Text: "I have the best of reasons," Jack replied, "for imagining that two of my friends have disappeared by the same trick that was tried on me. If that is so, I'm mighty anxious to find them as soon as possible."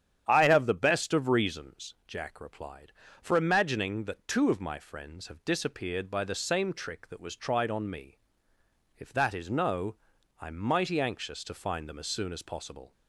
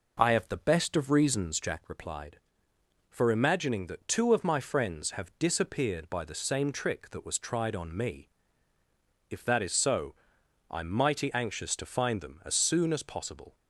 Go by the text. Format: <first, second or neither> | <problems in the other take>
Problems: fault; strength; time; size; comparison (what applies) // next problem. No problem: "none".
second | starts louder than the rest; strong; until 1.2 s; 9.5 dB // says "no" for "so"; at 9.4 s